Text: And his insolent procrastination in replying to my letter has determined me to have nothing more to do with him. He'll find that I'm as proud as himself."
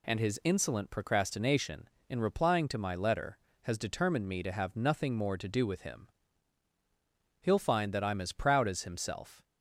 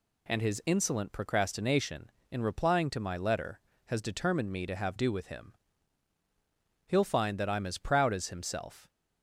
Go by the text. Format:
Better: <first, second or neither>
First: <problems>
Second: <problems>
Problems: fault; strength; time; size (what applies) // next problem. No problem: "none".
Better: first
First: none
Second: skips "nothing more to"; at 4.9 s